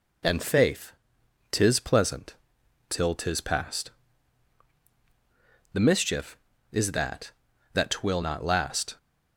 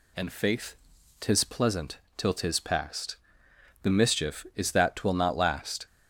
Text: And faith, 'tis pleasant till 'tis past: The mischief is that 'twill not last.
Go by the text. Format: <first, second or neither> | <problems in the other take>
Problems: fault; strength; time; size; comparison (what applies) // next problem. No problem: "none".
second | pauses between "pleasant" and "till"; noticeable; at 2.3 s; 0.52 s long; slight in the second // says "that" twice; at 7.7 s